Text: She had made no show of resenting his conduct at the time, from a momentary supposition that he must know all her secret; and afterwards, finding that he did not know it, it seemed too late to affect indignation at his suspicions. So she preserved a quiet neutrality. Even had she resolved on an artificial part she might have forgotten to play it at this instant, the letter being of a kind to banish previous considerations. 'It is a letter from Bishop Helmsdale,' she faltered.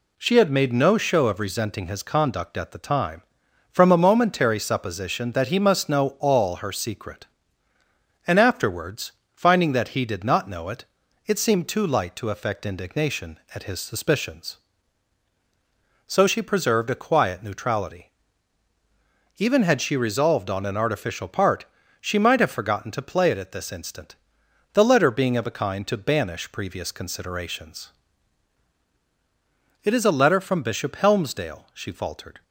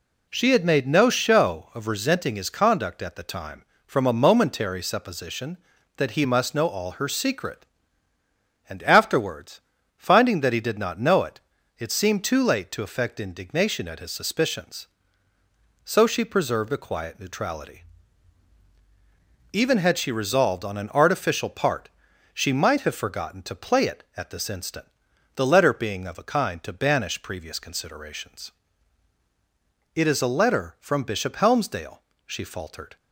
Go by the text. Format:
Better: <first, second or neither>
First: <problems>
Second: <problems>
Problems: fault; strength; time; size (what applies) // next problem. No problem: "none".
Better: second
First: says "light" for "late"; at 11.8 s // pauses between "part" and "she"; slight; at 21.6 s; 0.36 s long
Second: pauses between "part" and "she"; noticeable; at 21.8 s; 0.46 s long